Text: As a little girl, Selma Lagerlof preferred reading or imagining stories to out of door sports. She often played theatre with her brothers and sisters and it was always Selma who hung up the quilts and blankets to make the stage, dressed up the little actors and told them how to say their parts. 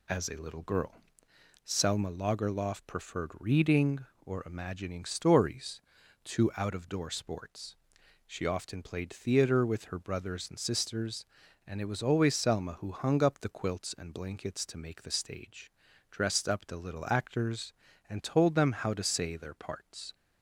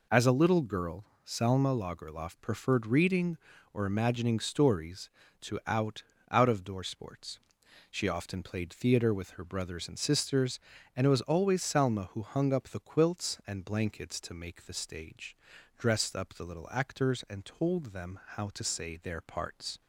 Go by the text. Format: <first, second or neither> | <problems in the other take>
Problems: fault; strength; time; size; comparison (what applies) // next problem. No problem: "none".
first | says "out" twice; at 6.3 s // pauses between "them" and "how"; slight; at 18.1 s; 0.18 s long